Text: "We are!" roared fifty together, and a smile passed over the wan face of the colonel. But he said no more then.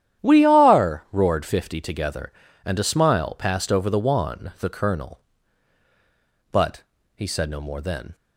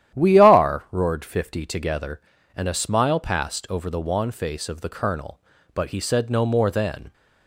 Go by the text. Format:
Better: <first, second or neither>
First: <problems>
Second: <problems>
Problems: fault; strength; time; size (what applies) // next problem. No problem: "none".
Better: second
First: starts louder than the rest; strong; until 1.2 s; 10.5 dB // skips "face of"; at 4.5 s // pauses between "But" and "he"; slight; at 6.8 s; 0.32 s long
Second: starts louder than the rest; strong; until 1.2 s; 11 dB